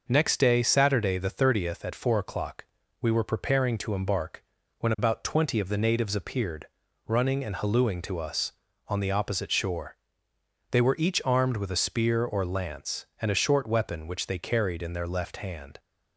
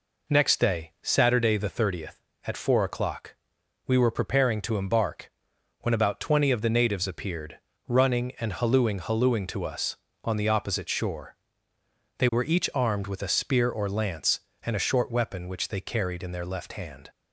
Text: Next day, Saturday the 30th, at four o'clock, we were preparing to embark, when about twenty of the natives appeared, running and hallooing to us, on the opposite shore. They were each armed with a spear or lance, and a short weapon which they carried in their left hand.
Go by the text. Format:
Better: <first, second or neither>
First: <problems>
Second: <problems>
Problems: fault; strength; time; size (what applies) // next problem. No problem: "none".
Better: first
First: none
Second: says "hallooing" twice; at 9.0 s